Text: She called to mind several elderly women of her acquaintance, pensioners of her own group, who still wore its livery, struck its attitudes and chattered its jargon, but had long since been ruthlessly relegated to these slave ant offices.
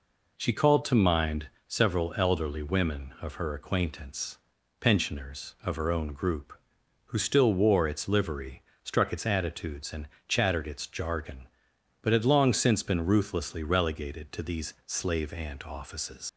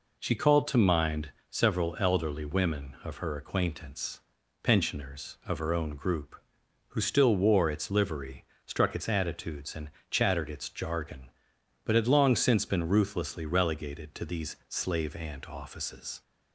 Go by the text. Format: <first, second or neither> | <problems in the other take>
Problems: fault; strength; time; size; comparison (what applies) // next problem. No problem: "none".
second | pauses between "mind" and "several"; slight; at 1.4 s; 0.18 s long; slight in the second // pauses between "and" and "chattered"; slight; at 10.0 s; 0.20 s long; slight in the second // leaves "offices" unfinished; at 16.2 s; 100 ms